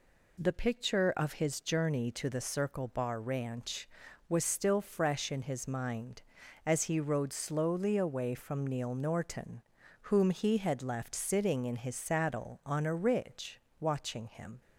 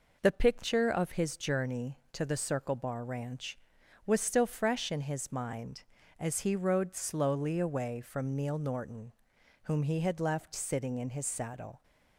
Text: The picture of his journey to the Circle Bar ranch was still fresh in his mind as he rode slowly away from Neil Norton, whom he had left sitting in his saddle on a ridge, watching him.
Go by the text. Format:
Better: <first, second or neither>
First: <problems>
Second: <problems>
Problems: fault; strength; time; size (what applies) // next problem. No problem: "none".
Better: first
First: none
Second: stops before "on a ridge watching him"; at 11.8 s